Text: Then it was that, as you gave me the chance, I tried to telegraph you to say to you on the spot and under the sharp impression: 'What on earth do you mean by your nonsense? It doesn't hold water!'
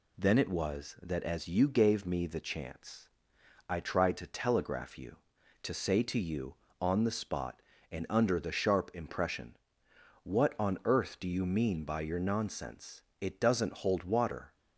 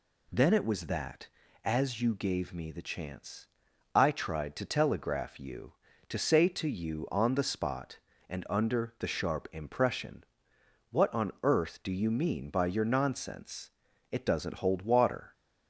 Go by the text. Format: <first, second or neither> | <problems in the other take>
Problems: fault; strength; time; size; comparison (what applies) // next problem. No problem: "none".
neither | none